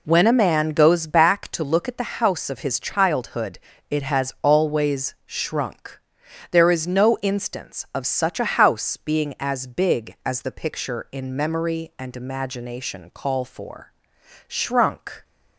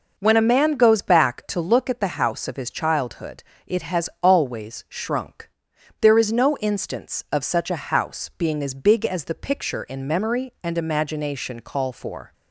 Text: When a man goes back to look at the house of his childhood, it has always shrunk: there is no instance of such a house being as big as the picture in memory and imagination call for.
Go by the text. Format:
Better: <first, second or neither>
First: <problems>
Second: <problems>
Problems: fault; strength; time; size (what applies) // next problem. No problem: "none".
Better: second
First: goes on to say "Shrunk"; noticeable; from 14.4 s on; 0.78 s long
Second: none